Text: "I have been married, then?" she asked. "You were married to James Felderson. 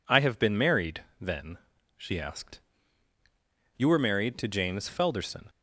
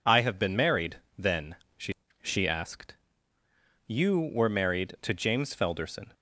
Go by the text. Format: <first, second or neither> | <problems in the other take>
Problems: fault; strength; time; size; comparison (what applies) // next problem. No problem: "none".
first | says "she" twice; at 2.2 s